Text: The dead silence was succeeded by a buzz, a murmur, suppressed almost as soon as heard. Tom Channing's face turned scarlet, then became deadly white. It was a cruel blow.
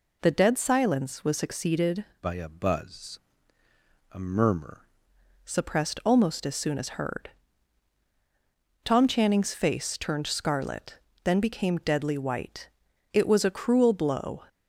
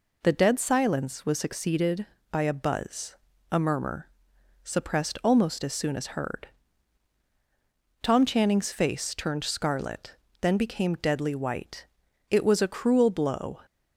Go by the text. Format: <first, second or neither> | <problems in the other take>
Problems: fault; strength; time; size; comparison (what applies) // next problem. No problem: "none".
second | changes voice from "by" to "murmur"; from 2.2 to 4.8 s; 2.6 s long